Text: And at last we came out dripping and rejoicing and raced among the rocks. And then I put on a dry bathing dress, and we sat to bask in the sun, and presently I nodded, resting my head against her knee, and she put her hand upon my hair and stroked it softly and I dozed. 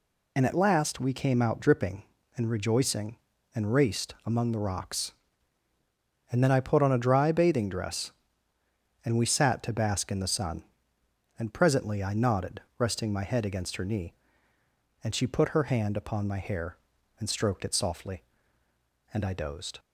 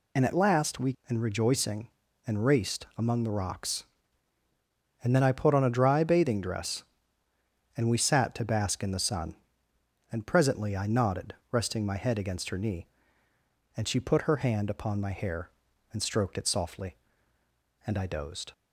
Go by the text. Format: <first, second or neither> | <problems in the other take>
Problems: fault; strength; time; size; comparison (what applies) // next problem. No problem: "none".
first | skips "came out dripping"; at 1.0 s